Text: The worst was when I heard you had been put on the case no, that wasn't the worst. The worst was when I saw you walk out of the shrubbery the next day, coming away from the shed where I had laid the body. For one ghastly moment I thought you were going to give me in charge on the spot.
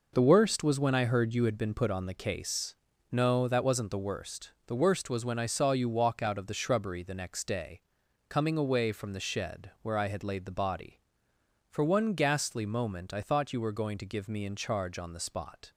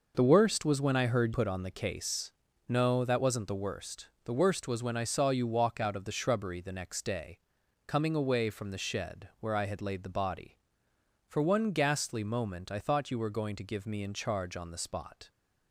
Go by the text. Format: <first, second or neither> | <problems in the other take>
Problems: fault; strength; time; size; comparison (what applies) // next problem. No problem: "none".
first | skips "you had been"; at 1.3 s // pauses between "case" and "no"; slight; at 2.3 s; 0.36 s long; slight in the first